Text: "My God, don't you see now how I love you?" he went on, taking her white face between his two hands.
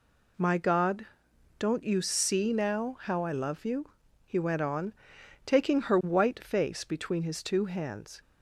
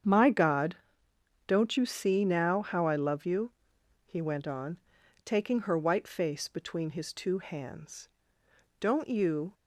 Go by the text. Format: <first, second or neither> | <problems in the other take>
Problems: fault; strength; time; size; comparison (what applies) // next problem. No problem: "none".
first | starts louder than the rest; strong; until 1.7 s; 8 dB // goes on to say "Don't you"; noticeable; from 8.8 s on; 0.72 s long